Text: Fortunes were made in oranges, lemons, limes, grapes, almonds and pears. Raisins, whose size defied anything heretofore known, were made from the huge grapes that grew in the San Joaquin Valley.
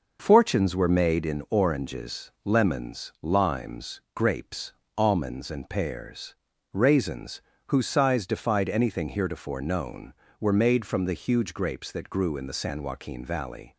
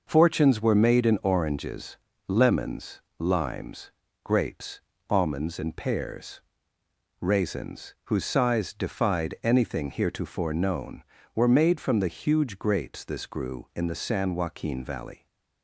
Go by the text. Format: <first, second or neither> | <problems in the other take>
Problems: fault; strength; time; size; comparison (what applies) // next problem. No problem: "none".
first | says "this" for "that"; at 13.0 s